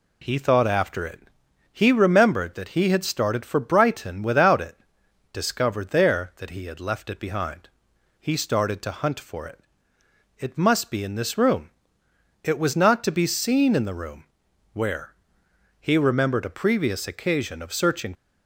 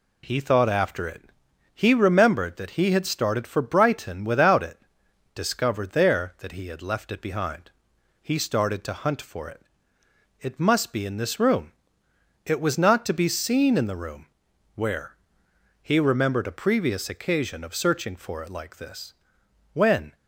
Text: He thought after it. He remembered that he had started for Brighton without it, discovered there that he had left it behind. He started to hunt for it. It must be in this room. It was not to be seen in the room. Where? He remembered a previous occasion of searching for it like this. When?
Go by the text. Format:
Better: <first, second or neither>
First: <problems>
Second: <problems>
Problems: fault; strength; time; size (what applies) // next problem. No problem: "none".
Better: second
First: stops before "for it like this When"; at 18.1 s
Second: none